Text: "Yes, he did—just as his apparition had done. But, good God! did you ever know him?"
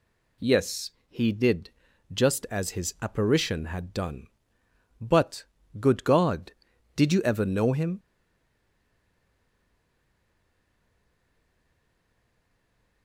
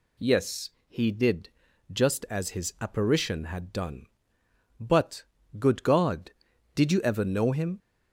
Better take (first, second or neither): second